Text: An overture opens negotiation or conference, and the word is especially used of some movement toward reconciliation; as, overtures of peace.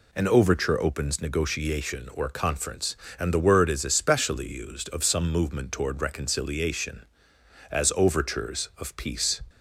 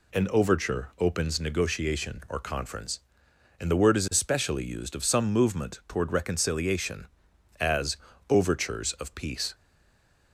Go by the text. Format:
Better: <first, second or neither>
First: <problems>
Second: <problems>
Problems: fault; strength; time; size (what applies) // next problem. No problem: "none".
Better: first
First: none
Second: stays silent after the last word; slight; from 9.5 s on; 0.8 s long